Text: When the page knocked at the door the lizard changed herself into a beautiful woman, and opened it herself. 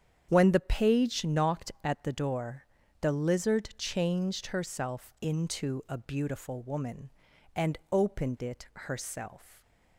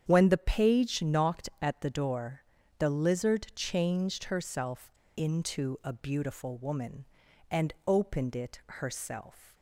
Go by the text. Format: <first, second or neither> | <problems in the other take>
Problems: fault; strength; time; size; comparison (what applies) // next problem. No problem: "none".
first | starts louder than the rest; strong; until 1.0 s; 8.5 dB; strong in the first // pauses between "door" and "the"; slight; at 2.4 s; 0.36 s long; slight in the first // pauses between "herself" and "into"; slight; at 4.8 s; 0.25 s long